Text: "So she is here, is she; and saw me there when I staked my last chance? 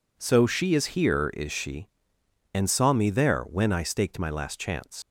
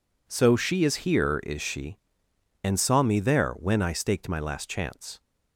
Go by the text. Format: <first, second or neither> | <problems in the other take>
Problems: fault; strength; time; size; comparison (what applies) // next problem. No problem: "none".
second | leaves "chance" unfinished; at 5.0 s; 80 ms